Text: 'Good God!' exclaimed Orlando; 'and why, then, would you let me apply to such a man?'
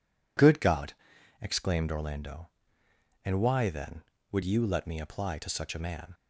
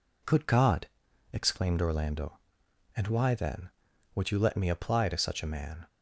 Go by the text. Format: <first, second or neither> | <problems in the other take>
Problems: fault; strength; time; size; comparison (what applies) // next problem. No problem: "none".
neither | none